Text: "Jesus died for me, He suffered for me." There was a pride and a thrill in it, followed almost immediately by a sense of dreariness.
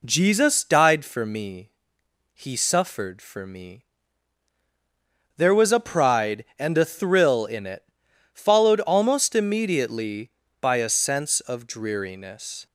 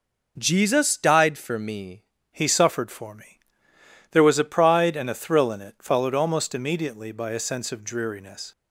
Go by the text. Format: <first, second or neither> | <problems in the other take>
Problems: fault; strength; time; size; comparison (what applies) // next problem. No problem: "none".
first | changes voice at "He"; from 2.3 s on; 6.2 s long